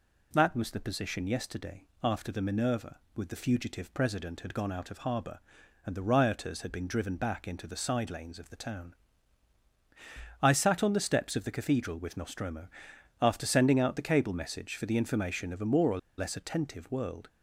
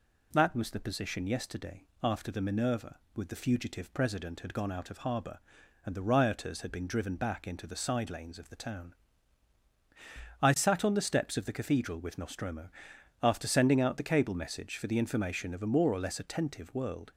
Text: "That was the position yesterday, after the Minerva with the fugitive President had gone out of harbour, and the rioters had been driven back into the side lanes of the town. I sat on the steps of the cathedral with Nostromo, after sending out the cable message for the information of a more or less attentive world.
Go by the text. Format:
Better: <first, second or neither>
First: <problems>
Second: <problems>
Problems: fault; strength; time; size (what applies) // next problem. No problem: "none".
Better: second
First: pauses between "or" and "less"; slight; at 15.9 s; 0.19 s long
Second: none